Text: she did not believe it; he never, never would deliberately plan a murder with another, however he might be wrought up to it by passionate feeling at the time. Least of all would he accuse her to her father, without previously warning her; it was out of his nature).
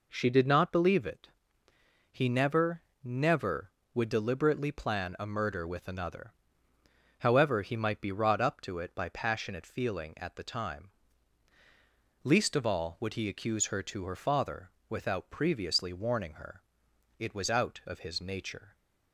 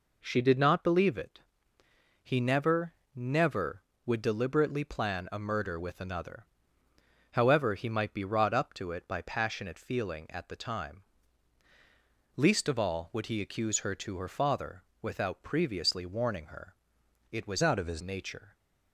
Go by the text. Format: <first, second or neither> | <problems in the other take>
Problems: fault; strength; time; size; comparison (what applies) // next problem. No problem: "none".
first | changes voice from "out" to "his"; from 17.6 to 18.0 s; 0.4 s long